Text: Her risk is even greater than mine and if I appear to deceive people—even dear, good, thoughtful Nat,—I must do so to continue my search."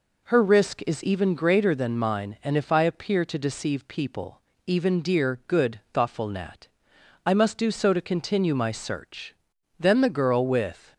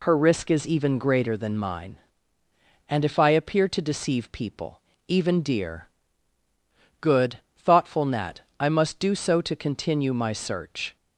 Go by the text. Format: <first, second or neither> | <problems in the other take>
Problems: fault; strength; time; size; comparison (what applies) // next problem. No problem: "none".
second | goes on to say "Then the girl with"; noticeable; from 9.7 s on; 1.1 s long